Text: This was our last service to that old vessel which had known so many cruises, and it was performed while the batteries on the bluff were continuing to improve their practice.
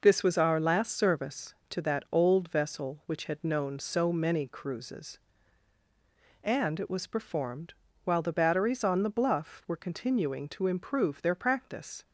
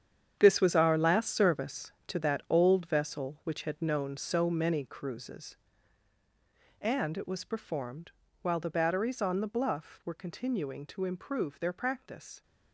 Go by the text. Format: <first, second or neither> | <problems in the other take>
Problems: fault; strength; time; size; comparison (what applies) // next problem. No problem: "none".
first | gets quieter; strong; throughout; 12 dB // pauses between "performed" and "while"; slight; at 8.0 s; 0.32 s long; slight in the first